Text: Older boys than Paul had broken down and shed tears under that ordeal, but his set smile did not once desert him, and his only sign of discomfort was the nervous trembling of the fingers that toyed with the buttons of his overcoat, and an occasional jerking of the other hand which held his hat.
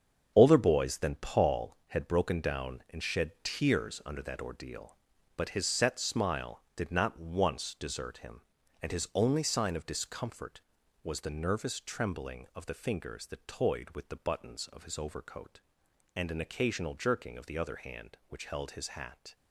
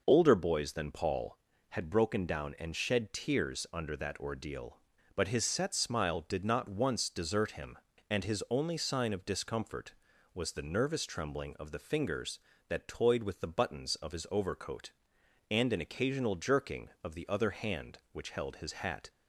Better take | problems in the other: second | gets quieter; strong; throughout; 9 dB

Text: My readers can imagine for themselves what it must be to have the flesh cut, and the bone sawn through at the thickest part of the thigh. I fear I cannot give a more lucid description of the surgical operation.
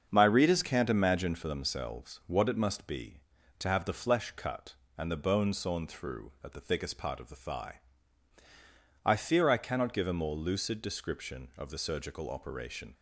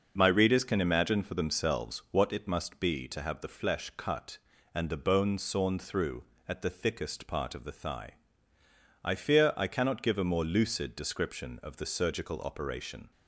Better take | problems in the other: second | starts louder than the rest; until 1.1 s; 6.5 dB // says "can't" for "can"; at 0.6 s

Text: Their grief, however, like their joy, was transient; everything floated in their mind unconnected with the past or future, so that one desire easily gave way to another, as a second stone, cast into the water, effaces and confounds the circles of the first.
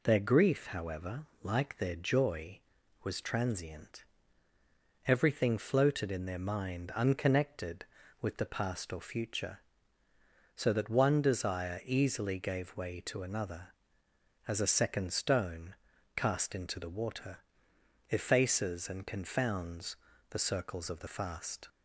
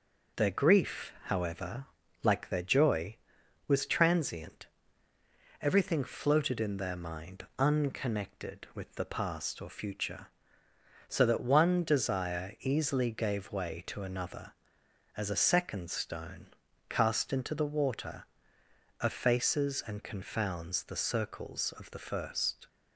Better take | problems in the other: second | pauses between "confounds" and "the"; slight; at 19.9 s; 0.32 s long // says "fast" for "first"; at 21.0 s

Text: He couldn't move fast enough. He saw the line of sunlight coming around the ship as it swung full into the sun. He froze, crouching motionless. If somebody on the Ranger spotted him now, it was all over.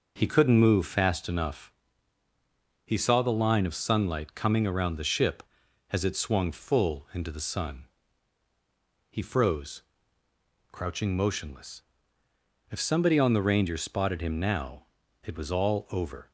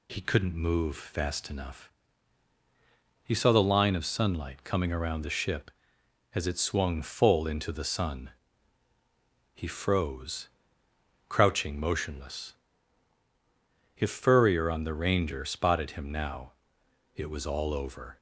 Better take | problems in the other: first | says "furrier" for "somebody"; at 14.1 s

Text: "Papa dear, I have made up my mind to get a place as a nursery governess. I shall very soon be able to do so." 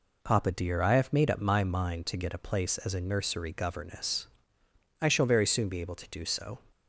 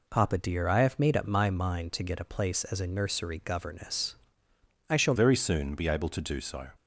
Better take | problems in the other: first | changes voice at "very"; from 5.1 s on; 1.5 s long

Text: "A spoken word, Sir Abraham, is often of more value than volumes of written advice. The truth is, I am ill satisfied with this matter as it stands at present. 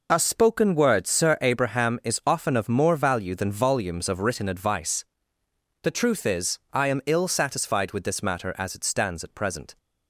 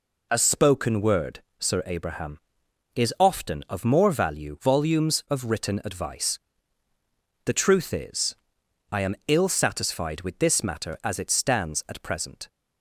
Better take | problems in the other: first | skips "than"; at 4.5 s

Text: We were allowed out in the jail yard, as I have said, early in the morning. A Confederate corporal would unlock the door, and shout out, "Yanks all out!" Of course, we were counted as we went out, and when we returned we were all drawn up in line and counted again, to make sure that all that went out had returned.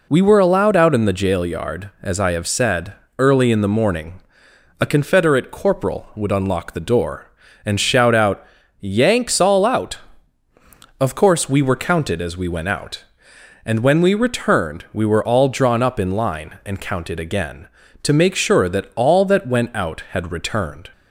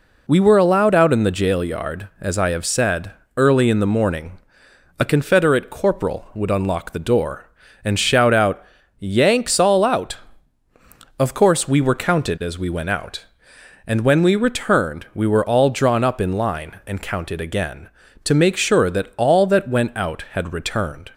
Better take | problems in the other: neither | none

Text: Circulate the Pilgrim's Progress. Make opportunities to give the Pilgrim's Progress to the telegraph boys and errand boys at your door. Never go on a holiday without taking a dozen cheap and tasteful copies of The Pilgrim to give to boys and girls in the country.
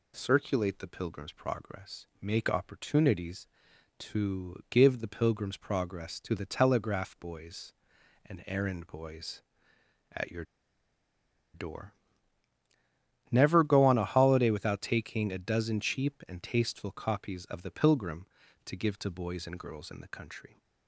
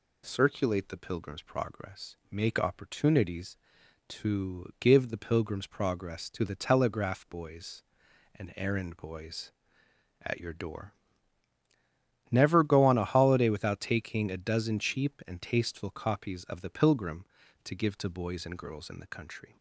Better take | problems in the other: second | pauses between "your" and "door"; at 10.4 s; 1.0 s long

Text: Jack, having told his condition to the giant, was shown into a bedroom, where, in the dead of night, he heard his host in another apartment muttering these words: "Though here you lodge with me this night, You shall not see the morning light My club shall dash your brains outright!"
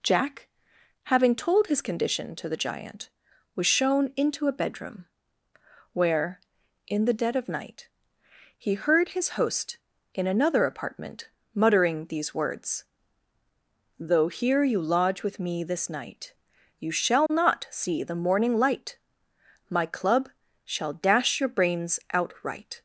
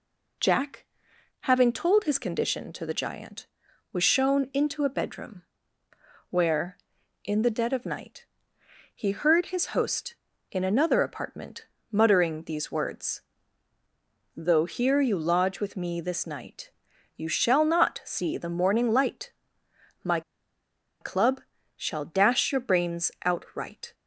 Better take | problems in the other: first | pauses between "apartment" and "muttering"; slight; at 11.6 s; 0.24 s long; slight in the first // pauses between "light" and "My"; noticeable; at 19.3 s; 0.72 s long; noticeable in the first // pauses between "My" and "club"; noticeable; at 20.2 s; 0.80 s long // pauses between "club" and "shall"; at 21.3 s; 0.38 s long; also in the first

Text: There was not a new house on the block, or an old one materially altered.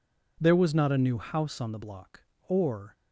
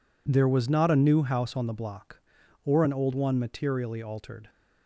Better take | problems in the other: second | stops before "an old one materially altered"; at 2.9 s

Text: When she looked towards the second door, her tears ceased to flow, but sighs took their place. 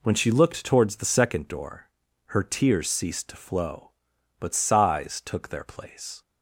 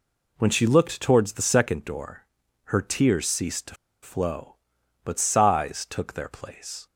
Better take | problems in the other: first | pauses between "to" and "flow"; slight; at 3.7 s; 0.28 s long

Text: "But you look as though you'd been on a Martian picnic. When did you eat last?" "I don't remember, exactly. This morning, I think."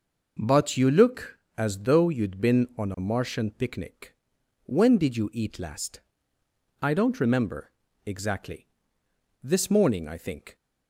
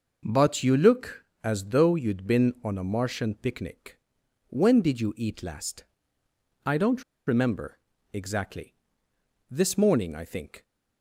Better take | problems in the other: first | pauses between "don't" and "remember"; slight; at 7.0 s; 0.24 s long

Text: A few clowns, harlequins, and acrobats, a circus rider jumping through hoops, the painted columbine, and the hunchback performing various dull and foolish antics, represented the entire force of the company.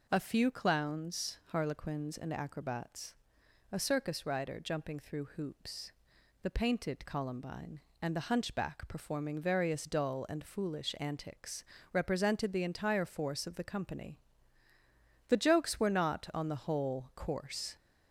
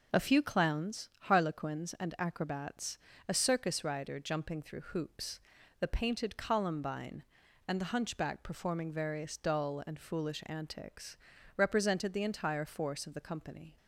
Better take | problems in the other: second | goes on to say "The jokes were not on the whole coarse"; strong; from 15.2 s on; 2.4 s long

